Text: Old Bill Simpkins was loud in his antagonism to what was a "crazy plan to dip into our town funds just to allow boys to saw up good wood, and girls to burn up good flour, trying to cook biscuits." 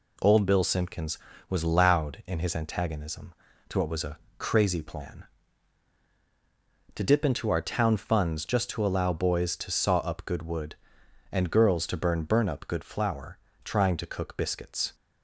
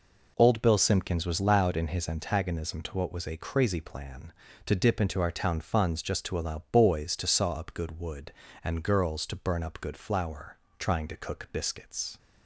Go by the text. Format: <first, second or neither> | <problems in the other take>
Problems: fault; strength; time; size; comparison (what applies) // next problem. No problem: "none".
second | pauses between "a" and "crazy"; slight; at 4.1 s; 0.22 s long // says "burn" twice; at 12.2 s